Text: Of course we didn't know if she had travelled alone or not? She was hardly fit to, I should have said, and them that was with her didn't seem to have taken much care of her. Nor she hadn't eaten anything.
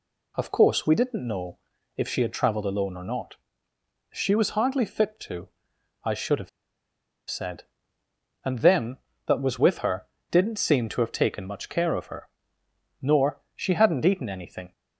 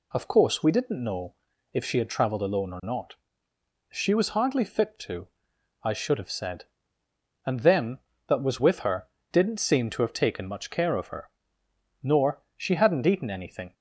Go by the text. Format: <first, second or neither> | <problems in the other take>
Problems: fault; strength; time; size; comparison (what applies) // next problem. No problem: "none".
second | pauses between "know" and "if"; at 1.5 s; 0.38 s long; also in the second // pauses between "have" and "said"; noticeable; at 6.4 s; 0.80 s long // pauses between "her" and "didn't"; slight; at 10.0 s; 0.24 s long; slight in the second